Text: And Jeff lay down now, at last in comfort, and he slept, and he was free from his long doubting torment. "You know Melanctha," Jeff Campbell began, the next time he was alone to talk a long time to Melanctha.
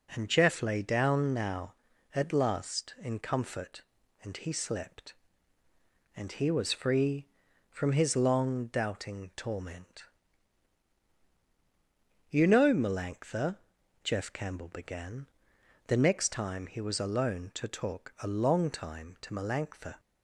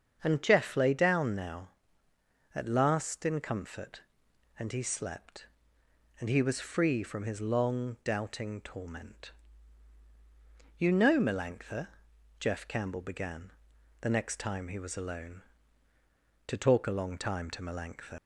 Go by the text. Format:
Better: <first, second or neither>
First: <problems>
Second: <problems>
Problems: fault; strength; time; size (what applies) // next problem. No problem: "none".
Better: first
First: none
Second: starts louder than the rest; until 1.2 s; 7 dB // leaves "Melanctha" unfinished; at 18.1 s; 105 ms